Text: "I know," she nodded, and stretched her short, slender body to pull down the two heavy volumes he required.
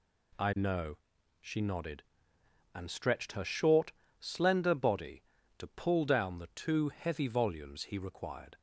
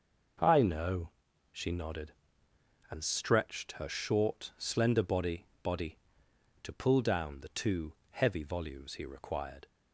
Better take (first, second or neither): first